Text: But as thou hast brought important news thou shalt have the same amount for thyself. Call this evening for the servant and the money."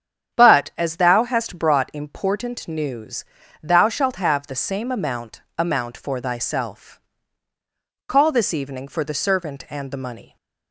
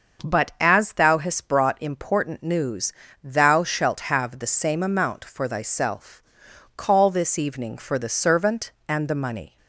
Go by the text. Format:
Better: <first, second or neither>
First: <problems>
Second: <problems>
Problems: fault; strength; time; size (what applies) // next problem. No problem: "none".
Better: second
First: starts louder than the rest; strong; until 1.4 s; 8.5 dB // pauses between "news" and "thou"; at 3.2 s; 0.38 s long // says "amount" twice; at 5.5 s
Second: starts louder than the rest; until 1.3 s; 6 dB // pauses between "news" and "thou"; slight; at 2.9 s; 0.32 s long